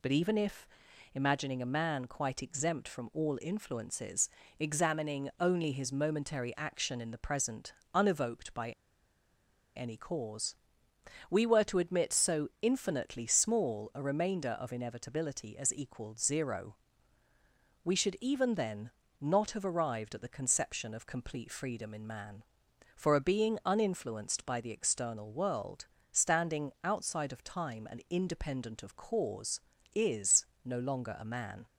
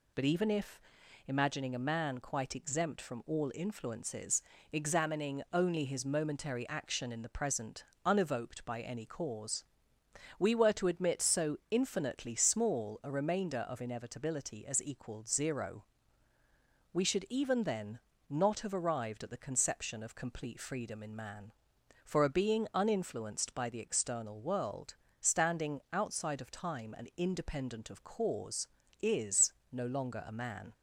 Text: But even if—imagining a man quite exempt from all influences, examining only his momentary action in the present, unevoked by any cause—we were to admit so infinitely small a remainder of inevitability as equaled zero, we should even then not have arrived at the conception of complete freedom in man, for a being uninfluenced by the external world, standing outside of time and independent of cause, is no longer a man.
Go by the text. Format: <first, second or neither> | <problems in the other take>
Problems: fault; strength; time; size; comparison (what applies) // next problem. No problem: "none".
second | pauses between "by" and "any"; at 8.7 s; 1.0 s long // pauses between "then" and "not"; slight; at 18.9 s; 0.30 s long; slight in the second // pauses between "is" and "no"; slight; at 30.4 s; 0.20 s long; slight in the second